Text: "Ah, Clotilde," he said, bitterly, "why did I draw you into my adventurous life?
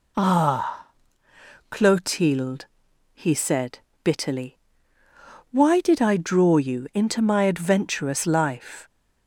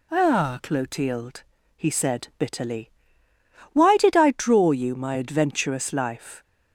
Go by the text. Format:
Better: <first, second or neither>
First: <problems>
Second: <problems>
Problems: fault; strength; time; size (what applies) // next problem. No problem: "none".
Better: first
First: none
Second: skips "into"; at 4.9 s